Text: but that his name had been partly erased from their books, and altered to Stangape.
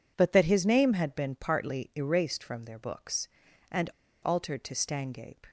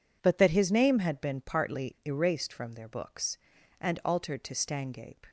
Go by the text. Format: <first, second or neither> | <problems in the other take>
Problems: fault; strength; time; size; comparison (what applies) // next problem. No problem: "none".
second | pauses between "and" and "altered"; slight; at 3.8 s; 0.33 s long